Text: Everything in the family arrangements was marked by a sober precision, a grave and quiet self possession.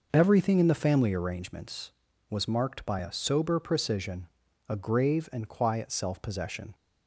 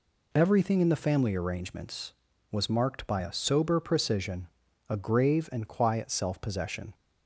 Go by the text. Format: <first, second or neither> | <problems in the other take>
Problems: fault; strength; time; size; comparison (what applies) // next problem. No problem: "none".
second | starts louder than the rest; noticeable; until 1.3 s; 5.5 dB